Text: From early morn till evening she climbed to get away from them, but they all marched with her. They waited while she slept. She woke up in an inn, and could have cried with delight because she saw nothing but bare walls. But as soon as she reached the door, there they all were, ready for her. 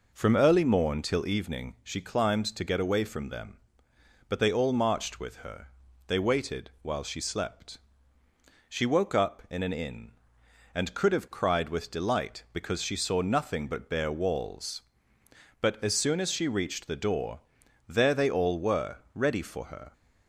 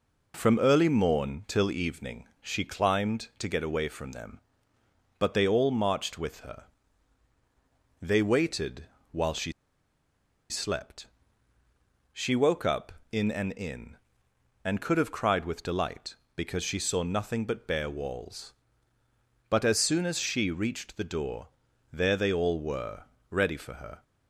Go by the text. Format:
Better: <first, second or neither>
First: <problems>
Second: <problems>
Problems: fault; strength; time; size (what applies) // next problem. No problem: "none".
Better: first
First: none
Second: pauses between "evening" and "she"; slight; at 2.2 s; 0.16 s long // pauses between "waited" and "while"; slight; at 8.8 s; 0.28 s long // pauses between "she" and "slept"; at 9.5 s; 0.98 s long